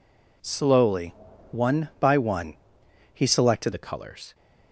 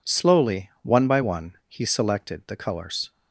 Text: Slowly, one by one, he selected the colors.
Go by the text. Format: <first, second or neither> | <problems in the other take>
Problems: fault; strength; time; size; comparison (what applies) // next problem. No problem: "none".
second | changes voice at "the"; from 3.7 s on; 0.6 s long